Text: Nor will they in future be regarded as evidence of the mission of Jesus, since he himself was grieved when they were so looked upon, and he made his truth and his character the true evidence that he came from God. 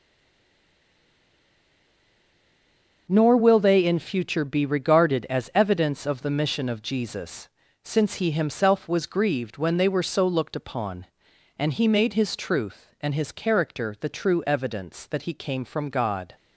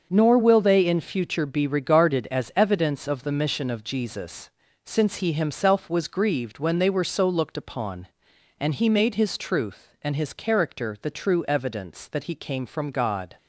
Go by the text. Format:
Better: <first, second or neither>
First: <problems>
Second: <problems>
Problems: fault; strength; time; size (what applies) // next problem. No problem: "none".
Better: second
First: stays silent before the first word; strong; until 3.0 s; 3.0 s long // starts louder than the rest; until 4.1 s; 6.5 dB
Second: starts louder than the rest; until 1.1 s; 6.5 dB